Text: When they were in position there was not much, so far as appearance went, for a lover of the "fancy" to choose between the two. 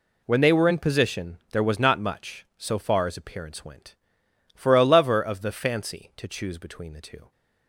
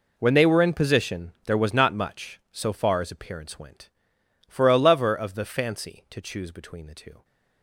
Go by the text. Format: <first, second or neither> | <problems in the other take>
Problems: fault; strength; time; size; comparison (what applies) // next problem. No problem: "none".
first | gets quieter; strong; throughout; 16 dB